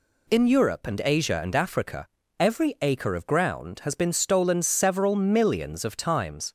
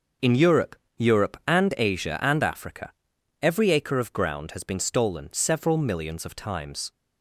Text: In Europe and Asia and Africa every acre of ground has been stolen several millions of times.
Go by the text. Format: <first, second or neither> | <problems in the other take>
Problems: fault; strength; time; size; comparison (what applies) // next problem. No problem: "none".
first | says "Europe" twice; at 0.9 s // pauses between "Africa" and "every"; noticeable; at 2.9 s; 0.50 s long; slight in the first